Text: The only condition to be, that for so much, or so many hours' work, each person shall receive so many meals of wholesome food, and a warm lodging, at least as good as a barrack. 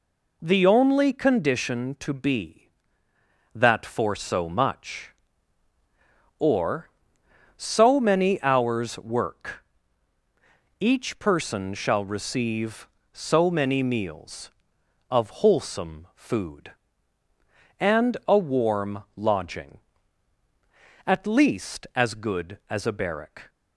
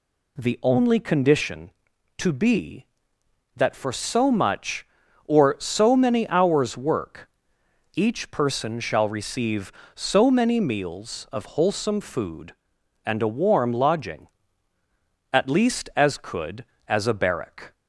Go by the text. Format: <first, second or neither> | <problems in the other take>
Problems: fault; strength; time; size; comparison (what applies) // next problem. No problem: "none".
first | says "could" for "good"; at 16.1 s